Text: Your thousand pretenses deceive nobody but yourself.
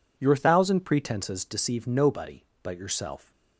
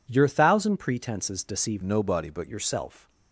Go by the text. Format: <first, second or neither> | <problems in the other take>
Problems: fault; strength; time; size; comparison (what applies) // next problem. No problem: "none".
first | changes voice from "nobody" to "but"; from 1.8 to 2.4 s; 0.6 s long